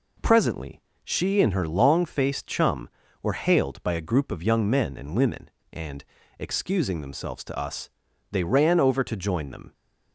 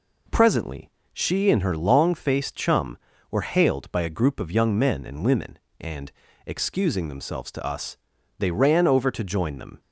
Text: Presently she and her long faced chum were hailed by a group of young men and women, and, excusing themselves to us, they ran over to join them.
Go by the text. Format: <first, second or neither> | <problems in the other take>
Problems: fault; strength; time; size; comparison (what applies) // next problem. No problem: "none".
neither | pauses between "Presently" and "she"; slight; the same in both